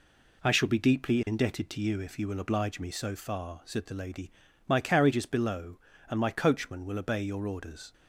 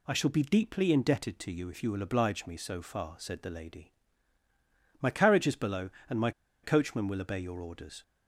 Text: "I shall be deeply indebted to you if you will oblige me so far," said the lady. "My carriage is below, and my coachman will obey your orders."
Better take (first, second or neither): first